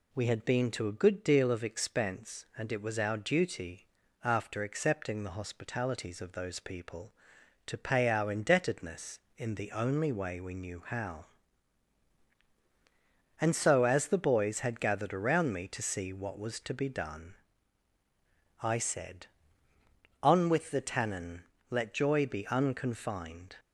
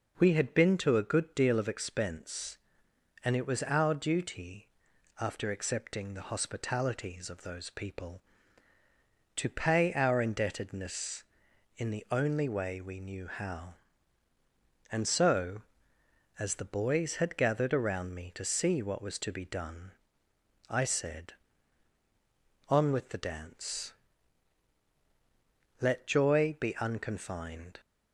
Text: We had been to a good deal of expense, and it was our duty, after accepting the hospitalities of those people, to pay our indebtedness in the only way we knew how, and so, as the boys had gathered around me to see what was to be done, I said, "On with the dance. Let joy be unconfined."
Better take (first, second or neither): second